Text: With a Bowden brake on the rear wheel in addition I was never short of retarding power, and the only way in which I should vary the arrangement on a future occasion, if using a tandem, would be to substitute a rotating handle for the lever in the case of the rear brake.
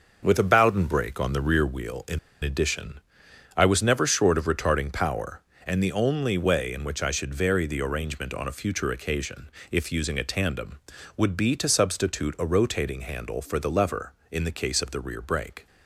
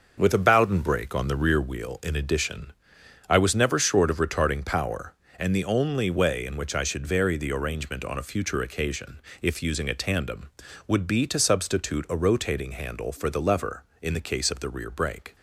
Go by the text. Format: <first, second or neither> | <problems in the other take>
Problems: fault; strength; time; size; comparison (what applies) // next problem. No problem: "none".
second | starts louder than the rest; noticeable; until 1.2 s; 6 dB; noticeable in the second // pauses between "in" and "addition"; slight; at 2.1 s; 0.24 s long // pauses between "addition" and "I"; noticeable; at 3.0 s; 0.56 s long; noticeable in the second